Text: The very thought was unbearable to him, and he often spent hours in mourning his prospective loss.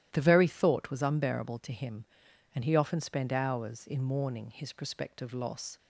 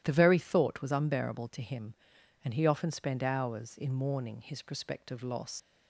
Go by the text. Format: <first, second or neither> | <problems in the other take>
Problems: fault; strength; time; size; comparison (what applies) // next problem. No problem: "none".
first | starts louder than the rest; strong; until 1.0 s; 12.5 dB; strong in the first // leaves "loss" unfinished; at 5.5 s; 70 ms